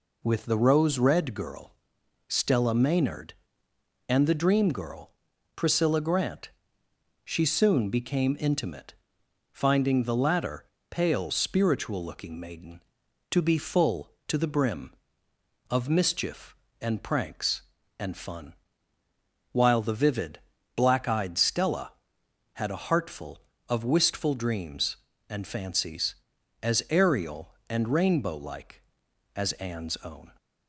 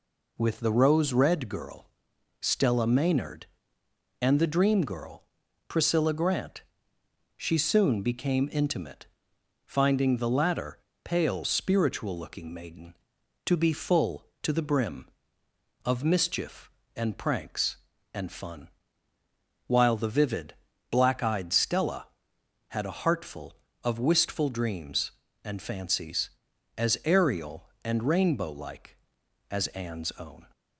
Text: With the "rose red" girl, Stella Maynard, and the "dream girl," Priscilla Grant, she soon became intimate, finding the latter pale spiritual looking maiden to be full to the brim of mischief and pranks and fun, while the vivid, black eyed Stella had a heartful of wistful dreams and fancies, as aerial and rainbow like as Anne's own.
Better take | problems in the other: neither | pauses between "latter" and "pale"; slight; the same in both

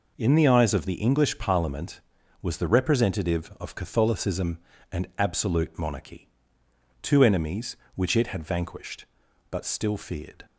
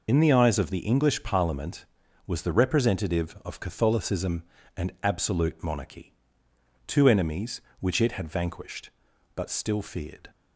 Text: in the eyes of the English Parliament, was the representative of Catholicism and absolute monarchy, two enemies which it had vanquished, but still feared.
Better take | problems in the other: first | loses the start of "in"; at 0.0 s; 75 ms

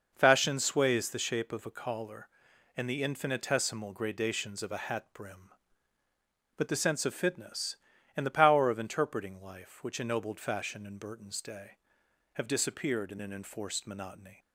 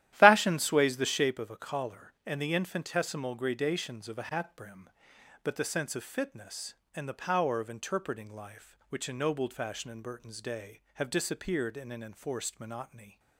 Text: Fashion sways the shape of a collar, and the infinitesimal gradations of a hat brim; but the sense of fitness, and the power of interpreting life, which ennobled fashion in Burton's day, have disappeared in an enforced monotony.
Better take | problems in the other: first | starts louder than the rest; strong; until 1.4 s; 13 dB

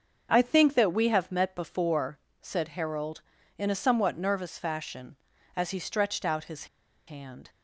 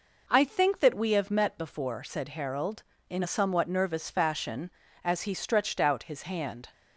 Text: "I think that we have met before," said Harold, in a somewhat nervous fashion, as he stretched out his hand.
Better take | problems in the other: second | starts louder than the rest; until 1.3 s; 6.5 dB // pauses between "his" and "hand"; at 6.6 s; 0.41 s long

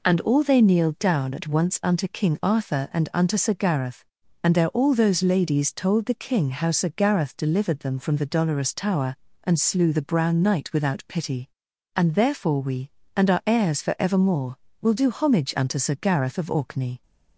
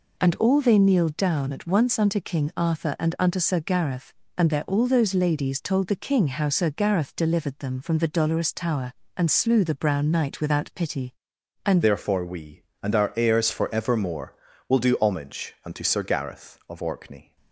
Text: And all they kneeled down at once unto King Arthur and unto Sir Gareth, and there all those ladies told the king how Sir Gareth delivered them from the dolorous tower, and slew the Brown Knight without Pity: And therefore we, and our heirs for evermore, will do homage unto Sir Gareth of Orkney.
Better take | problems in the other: first | changes voice at "therefore"; from 11.8 s on; 5.5 s long

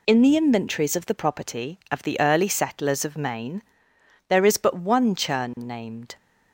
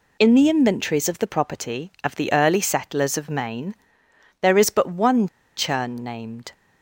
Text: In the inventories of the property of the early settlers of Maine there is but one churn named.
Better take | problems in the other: first | pauses between "Maine" and "there"; noticeable; at 3.7 s; 0.66 s long; noticeable in the first // pauses between "one" and "churn"; slight; at 5.2 s; 0.29 s long

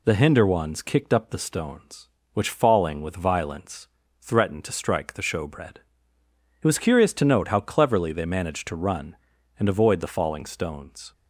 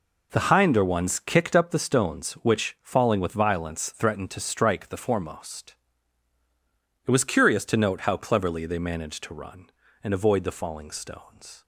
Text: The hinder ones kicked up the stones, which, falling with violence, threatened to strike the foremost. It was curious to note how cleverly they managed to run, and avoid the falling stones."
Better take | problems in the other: second | says "showbread" for "foremost"; at 5.2 s

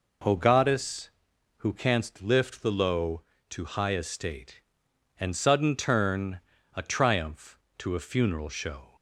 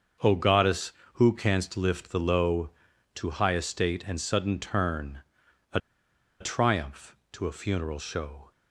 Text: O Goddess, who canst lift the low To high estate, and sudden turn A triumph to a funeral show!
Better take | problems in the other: first | starts louder than the rest; until 1.4 s; 6.5 dB // pauses between "turn" and "A"; noticeable; at 5.2 s; 0.52 s long; slight in the first // pauses between "A" and "triumph"; noticeable; at 5.7 s; 0.61 s long

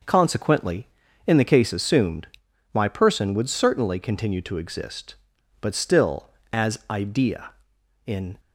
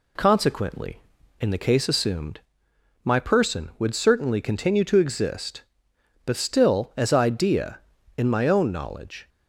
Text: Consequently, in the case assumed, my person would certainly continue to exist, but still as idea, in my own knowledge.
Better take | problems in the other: second | stops before "my own knowledge"; at 8.3 s

